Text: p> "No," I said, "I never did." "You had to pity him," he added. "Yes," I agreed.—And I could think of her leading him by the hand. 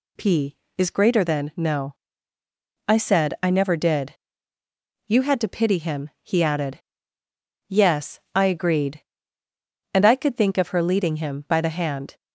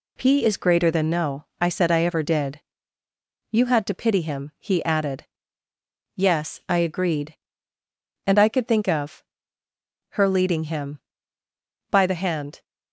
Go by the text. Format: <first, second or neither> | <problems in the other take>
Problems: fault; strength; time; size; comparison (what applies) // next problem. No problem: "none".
first | says "ever" for "never"; at 2.0 s // pauses between "of" and "her"; noticeable; at 9.2 s; 0.90 s long